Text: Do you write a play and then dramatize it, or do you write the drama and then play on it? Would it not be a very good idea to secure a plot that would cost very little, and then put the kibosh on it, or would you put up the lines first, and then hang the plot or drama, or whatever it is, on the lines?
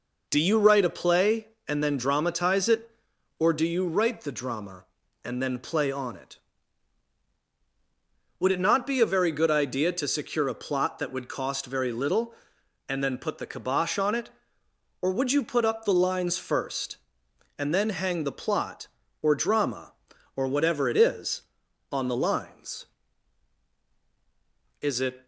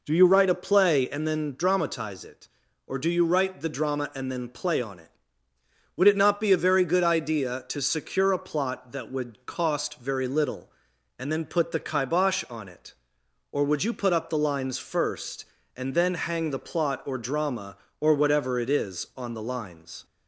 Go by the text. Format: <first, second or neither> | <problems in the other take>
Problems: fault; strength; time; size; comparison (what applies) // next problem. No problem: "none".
second | goes on to say "Is it"; slight; from 24.8 s on; 0.44 s long